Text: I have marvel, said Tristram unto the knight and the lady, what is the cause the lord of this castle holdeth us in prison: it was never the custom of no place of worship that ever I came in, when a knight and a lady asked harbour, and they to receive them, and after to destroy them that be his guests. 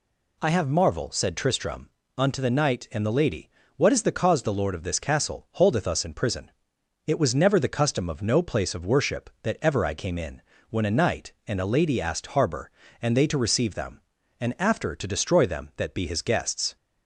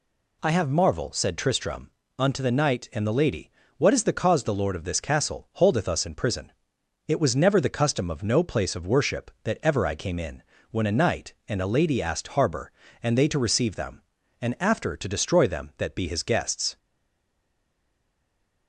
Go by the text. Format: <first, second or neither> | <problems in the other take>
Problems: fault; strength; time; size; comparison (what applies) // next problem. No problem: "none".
first | pauses between "Tristram" and "unto"; slight; at 1.9 s; 0.26 s long; slight in the first // stays silent after the last word; noticeable; from 16.7 s on; 1.9 s long